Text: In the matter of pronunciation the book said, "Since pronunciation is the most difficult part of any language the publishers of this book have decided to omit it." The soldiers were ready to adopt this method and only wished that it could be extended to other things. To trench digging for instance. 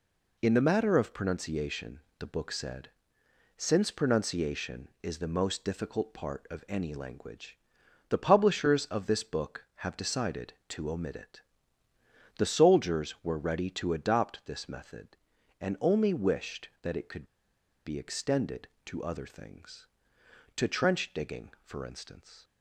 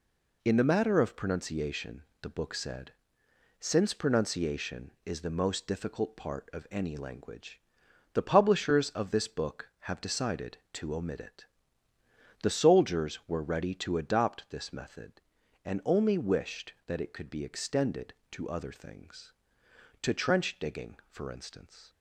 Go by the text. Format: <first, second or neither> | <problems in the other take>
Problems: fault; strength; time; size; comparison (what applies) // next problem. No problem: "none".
second | pauses between "pronunciation" and "the"; slight; at 1.9 s; 0.20 s long; slight in the second // pauses between "language" and "the"; noticeable; at 7.5 s; 0.52 s long; noticeable in the second // pauses between "could" and "be"; noticeable; at 17.2 s; 0.60 s long